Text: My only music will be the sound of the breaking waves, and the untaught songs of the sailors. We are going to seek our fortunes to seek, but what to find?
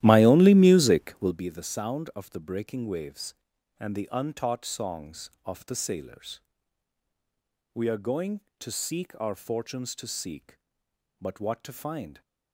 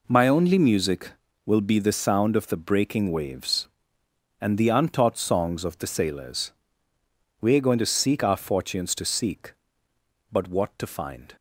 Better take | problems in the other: second | starts louder than the rest; strong; until 1.5 s; 13.5 dB

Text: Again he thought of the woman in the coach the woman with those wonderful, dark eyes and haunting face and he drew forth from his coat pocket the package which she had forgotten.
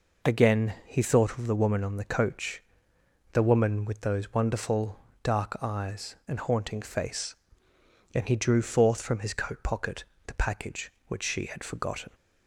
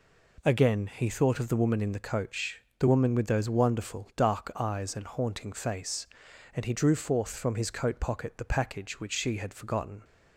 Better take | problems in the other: second | says "on" for "in"; at 1.8 s // pauses between "coach" and "the"; noticeable; at 2.6 s; 0.70 s long; slight in the second // pauses between "pocket" and "the"; slight; at 10.0 s; 0.22 s long

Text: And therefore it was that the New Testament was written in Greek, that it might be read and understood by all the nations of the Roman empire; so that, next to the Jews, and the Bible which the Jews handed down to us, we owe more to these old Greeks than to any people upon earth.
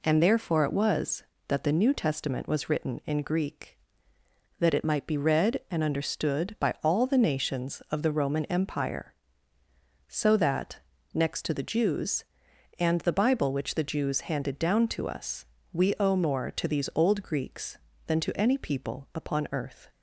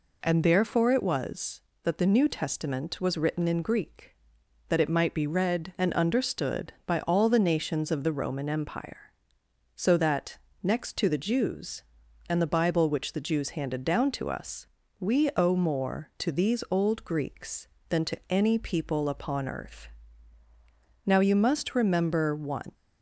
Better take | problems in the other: first | goes on to say "Now you must remember one"; strong; from 21.0 s on; 1.6 s long

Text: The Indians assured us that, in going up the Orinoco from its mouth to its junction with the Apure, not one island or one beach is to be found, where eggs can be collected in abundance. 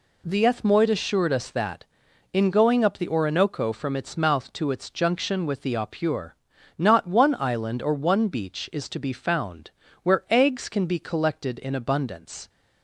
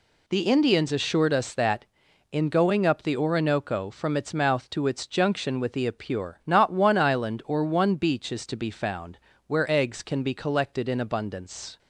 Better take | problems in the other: second | says "Ethmoid" for "Indians"; at 0.4 s

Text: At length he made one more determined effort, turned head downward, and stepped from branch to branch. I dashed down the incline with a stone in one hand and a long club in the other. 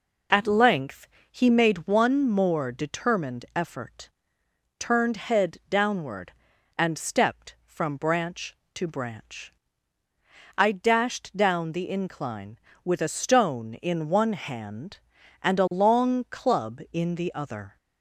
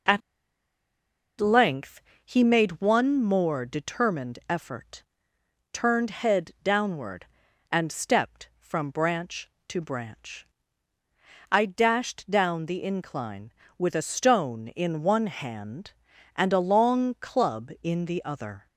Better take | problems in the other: first | pauses between "At" and "length"; at 0.2 s; 1.2 s long // pauses between "length" and "he"; slight; at 2.0 s; 0.22 s long; slight in the first

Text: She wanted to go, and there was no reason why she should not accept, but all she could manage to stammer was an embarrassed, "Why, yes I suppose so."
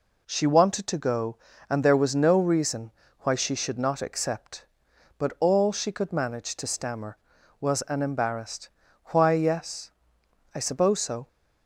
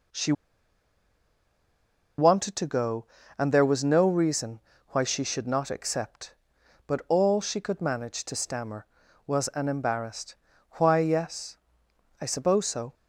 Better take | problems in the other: first | pauses between "She" and "wanted"; strong; at 0.3 s; 1.8 s long // pauses between "reason" and "why"; slight; at 4.5 s; 0.30 s long; slight in the first // pauses between "yes" and "I"; noticeable; at 11.5 s; 0.62 s long; noticeable in the first

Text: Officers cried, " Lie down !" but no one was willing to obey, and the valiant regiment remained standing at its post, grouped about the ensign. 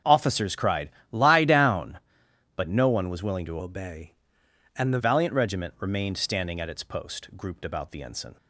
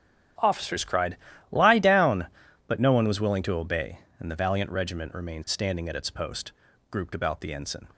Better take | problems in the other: second | starts louder than the rest; until 1.1 s; 7 dB // changes voice from "obey" to "the"; from 3.5 to 4.9 s; 1.4 s long

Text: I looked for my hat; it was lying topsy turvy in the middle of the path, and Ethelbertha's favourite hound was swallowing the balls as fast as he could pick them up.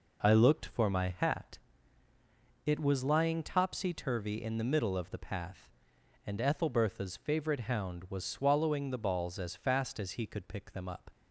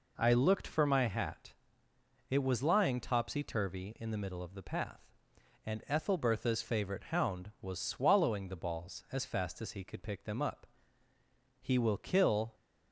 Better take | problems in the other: first | goes on to say "He will kill"; noticeable; from 11.6 s on; 0.94 s long

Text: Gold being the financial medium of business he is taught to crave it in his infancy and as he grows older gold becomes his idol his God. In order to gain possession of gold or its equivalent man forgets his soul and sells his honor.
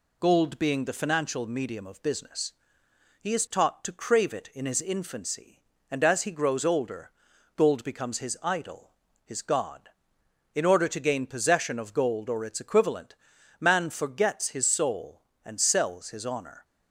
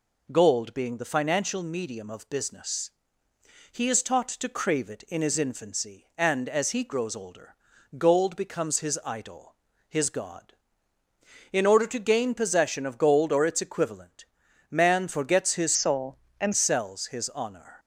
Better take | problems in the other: first | pauses between "business" and "he"; noticeable; at 2.9 s; 0.82 s long; noticeable in the first // pauses between "older" and "gold"; at 7.5 s; 0.42 s long; noticeable in the first // pauses between "idol" and "his"; slight; at 9.5 s; 0.34 s long; slight in the first // pauses between "equivalent" and "man"; noticeable; at 14.2 s; 0.46 s long; also in the first // changes voice from "soul" to "and"; from 15.7 to 16.5 s; 0.8 s long

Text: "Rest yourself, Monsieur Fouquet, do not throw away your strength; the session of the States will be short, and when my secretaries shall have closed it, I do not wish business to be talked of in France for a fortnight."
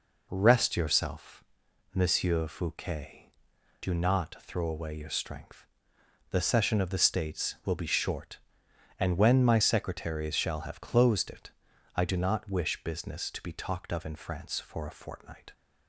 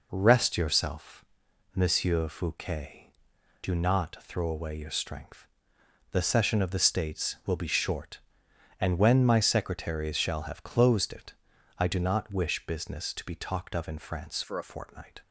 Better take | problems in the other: first | changes voice from "for" to "a"; from 14.4 to 14.6 s; 0.2 s long

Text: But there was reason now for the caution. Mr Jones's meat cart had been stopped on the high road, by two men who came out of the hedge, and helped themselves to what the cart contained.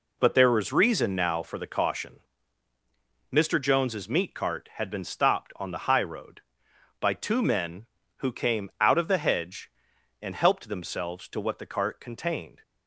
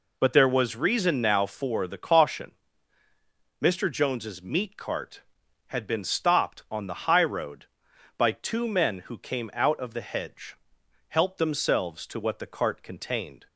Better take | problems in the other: first | skips "and"; at 10.8 s

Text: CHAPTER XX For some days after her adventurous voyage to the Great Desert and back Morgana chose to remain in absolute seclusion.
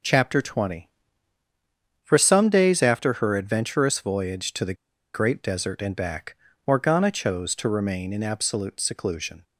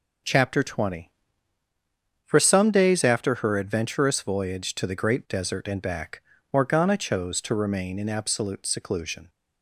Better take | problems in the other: second | pauses between "the" and "Great"; at 4.7 s; 0.40 s long // pauses between "back" and "Morgana"; slight; at 6.3 s; 0.30 s long; slight in the second

